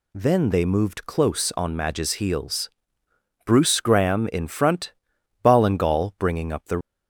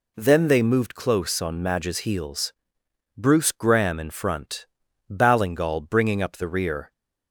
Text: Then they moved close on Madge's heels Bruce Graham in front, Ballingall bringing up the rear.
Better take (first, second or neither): second